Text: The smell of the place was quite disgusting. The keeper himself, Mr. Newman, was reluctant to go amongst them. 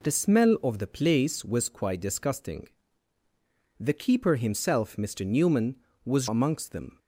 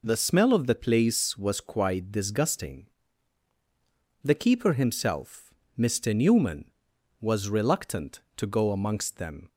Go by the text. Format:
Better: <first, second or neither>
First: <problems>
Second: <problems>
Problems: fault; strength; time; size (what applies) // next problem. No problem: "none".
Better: second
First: skips "reluctant to go"; at 6.2 s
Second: none